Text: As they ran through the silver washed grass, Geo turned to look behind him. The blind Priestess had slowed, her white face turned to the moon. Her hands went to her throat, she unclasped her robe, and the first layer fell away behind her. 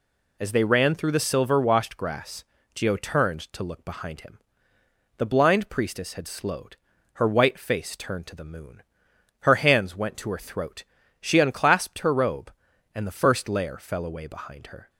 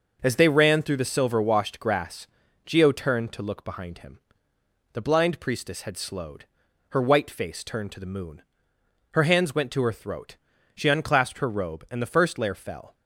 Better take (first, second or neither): first